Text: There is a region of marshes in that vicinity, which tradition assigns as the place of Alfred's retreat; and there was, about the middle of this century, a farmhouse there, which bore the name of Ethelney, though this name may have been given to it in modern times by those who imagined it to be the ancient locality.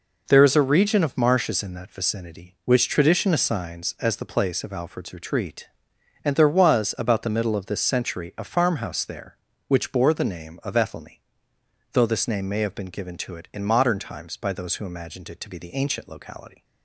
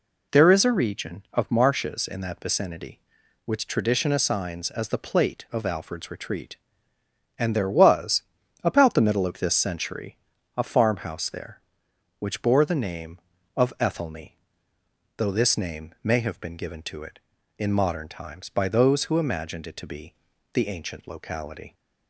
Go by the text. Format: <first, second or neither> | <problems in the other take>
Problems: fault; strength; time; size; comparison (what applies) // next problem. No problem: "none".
first | says "plate" for "place"; at 4.9 s // pauses between "be" and "the"; at 20.1 s; 0.40 s long